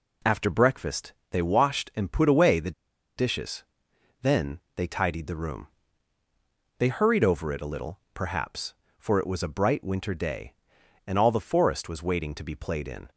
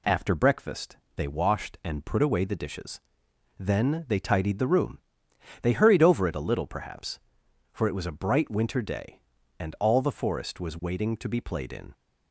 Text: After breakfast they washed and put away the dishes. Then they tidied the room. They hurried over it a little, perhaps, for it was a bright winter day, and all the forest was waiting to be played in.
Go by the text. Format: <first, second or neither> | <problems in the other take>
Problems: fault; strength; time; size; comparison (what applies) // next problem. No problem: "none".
second | pauses between "breakfast" and "they"; slight; at 1.1 s; 0.18 s long; slight in the second // pauses between "the" and "dishes"; noticeable; at 2.7 s; 0.46 s long // pauses between "Then" and "they"; slight; at 4.5 s; 0.16 s long